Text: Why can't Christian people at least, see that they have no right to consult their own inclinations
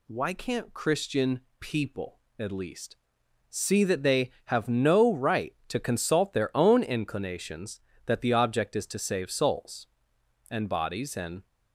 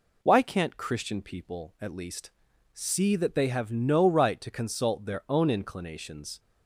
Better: second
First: pauses between "Christian" and "people"; slight; at 1.4 s; 0.18 s long // goes on to say "that the object is to save souls and bodies and"; strong; from 8.0 s on; 3.4 s long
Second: none

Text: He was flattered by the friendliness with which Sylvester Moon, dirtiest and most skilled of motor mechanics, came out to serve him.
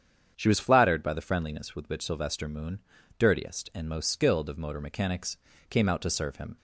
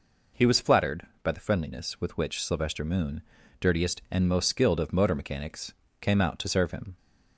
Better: second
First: starts louder than the rest; strong; until 1.3 s; 8 dB // says "She" for "He"; at 0.3 s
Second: none

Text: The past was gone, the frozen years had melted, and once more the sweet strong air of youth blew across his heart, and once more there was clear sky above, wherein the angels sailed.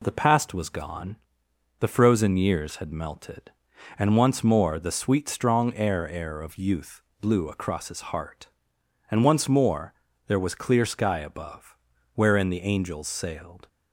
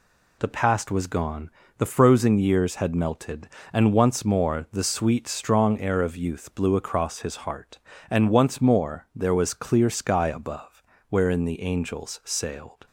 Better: second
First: says "air" twice; at 6.0 s // pauses between "youth" and "blew"; slight; at 7.0 s; 0.18 s long // pauses between "more" and "there"; slight; at 9.9 s; 0.36 s long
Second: none

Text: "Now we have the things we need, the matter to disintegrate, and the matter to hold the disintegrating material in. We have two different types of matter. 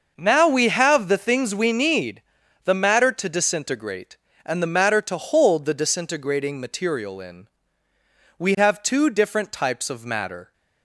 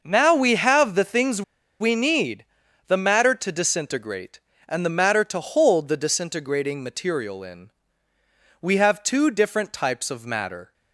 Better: first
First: starts louder than the rest; noticeable; until 1.1 s; 6 dB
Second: starts louder than the rest; noticeable; until 1.0 s; 6 dB // pauses between "things" and "we"; at 1.4 s; 0.39 s long

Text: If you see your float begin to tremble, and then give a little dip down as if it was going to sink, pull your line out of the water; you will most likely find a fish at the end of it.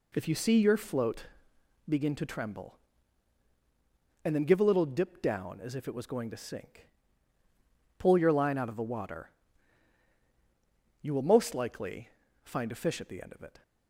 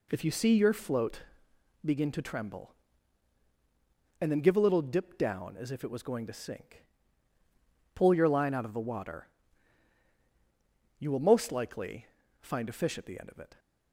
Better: neither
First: pauses between "float" and "begin"; noticeable; at 1.2 s; 0.66 s long // pauses between "likely" and "find"; slight; at 12.1 s; 0.34 s long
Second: pauses between "float" and "begin"; noticeable; at 1.1 s; 0.66 s long // pauses between "likely" and "find"; slight; at 12.0 s; 0.34 s long

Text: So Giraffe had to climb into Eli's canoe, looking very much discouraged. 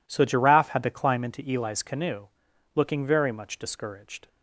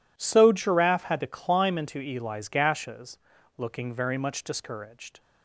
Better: first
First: none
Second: says "gashes" for "canoe"; at 2.4 s

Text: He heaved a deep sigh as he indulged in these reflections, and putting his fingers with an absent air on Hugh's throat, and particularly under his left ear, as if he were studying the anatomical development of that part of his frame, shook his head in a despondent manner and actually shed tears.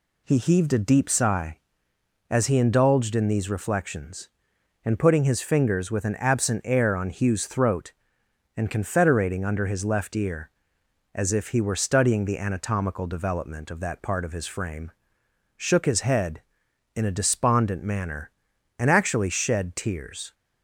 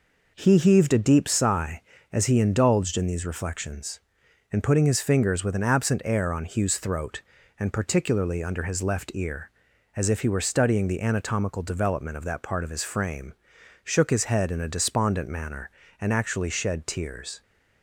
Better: second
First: says "confederating" for "particularly"; at 8.6 s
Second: none

